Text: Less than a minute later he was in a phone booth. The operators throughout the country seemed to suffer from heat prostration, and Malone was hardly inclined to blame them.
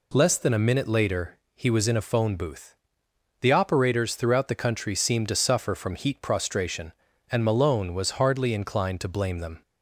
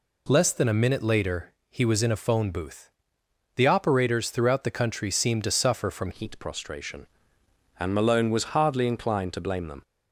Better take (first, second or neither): first